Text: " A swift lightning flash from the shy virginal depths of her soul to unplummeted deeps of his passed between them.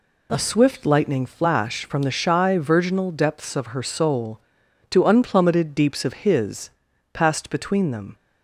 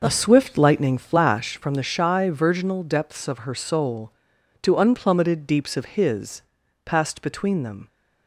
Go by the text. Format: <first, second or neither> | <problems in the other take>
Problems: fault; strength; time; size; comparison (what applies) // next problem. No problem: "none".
first | starts louder than the rest; noticeable; until 1.5 s; 6 dB // pauses between "his" and "passed"; at 6.4 s; 0.42 s long; also in the first